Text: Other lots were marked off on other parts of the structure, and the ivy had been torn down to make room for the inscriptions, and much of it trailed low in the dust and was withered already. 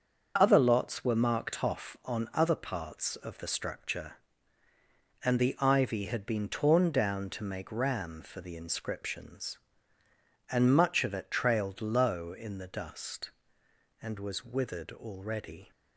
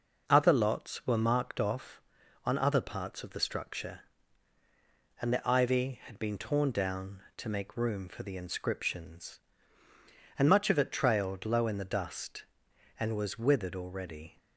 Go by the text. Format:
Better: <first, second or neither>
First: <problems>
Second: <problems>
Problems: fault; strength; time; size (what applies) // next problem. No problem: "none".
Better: second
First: starts louder than the rest; until 1.3 s; 6.5 dB // says "ram" for "room"; at 7.7 s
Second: none